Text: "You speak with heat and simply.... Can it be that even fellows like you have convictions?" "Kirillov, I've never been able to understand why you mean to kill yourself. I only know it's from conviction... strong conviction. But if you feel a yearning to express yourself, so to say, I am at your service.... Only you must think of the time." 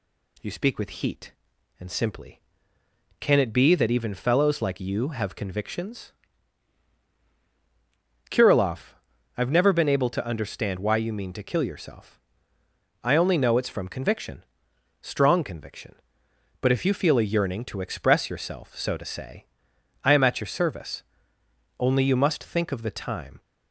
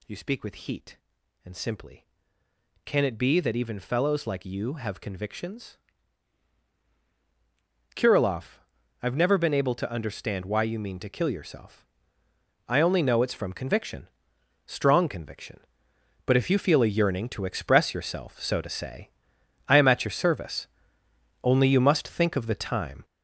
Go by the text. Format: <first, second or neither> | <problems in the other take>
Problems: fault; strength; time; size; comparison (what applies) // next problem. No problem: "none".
first | gets louder; strong; throughout; 8 dB